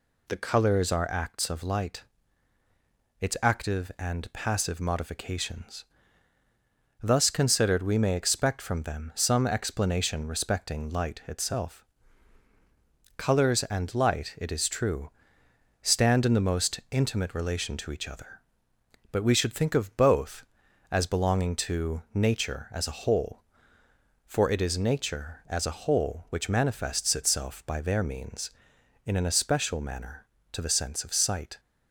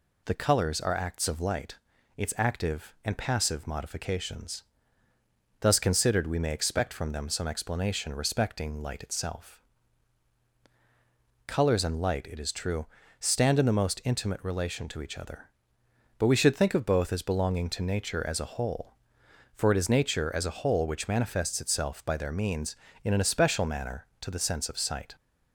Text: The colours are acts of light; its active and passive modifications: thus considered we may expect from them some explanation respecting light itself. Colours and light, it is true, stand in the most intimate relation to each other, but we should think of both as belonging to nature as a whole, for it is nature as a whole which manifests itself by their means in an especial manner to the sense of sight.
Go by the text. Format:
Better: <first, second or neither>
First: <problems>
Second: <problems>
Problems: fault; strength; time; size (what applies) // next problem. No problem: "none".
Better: neither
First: none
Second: none